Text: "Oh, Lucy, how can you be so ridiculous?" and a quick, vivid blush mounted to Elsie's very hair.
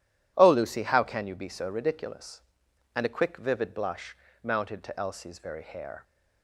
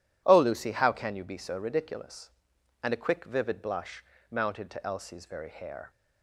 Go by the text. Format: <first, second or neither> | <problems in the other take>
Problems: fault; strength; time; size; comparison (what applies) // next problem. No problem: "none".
neither | pauses between "blush" and "mounted"; slight; the same in both